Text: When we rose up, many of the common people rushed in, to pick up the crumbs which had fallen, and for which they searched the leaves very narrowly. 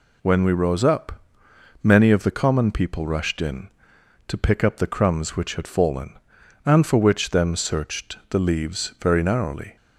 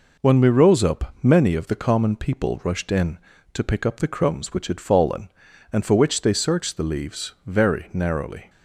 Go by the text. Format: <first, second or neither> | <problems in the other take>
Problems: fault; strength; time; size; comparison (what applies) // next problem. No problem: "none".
second | says "them" for "they"; at 7.2 s